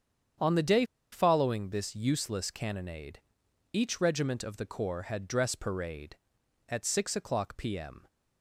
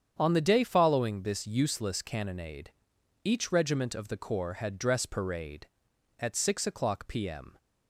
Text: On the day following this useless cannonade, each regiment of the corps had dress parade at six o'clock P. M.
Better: second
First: starts louder than the rest; strong; until 1.6 s; 8 dB // pauses between "day" and "following"; slight; at 0.8 s; 0.27 s long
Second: starts louder than the rest; strong; until 1.2 s; 8 dB

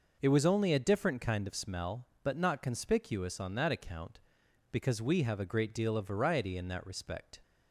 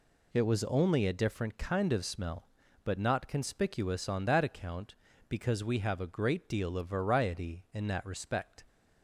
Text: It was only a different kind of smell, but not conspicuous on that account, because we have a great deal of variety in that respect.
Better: neither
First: none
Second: none

